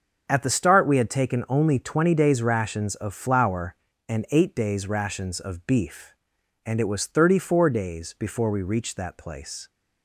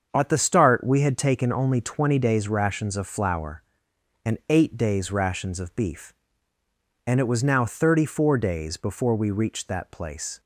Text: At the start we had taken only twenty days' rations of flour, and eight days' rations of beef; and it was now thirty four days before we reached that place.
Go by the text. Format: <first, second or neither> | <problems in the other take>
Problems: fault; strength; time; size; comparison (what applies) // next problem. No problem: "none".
second | starts louder than the rest; until 1.3 s; 6.5 dB; also in the second // skips "now"; at 7.0 s